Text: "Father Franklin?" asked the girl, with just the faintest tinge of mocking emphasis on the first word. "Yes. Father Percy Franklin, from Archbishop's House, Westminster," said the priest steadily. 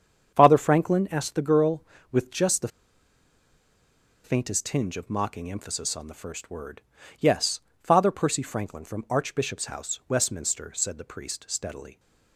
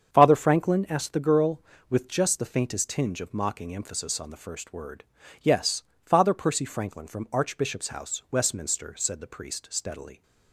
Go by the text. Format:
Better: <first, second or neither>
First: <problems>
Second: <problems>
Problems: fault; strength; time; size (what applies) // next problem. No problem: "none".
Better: second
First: starts louder than the rest; strong; until 1.3 s; 7.5 dB // pauses between "the" and "faintest"; strong; at 2.6 s; 1.5 s long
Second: starts louder than the rest; strong; until 1.1 s; 7.5 dB